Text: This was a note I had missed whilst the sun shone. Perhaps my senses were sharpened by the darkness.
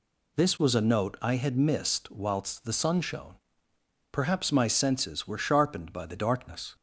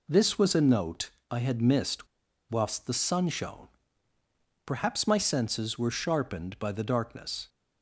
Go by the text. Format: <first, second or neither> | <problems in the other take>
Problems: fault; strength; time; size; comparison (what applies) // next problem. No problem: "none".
first | pauses between "note" and "I"; slight; at 1.1 s; 0.22 s long // pauses between "missed" and "whilst"; at 2.0 s; 0.43 s long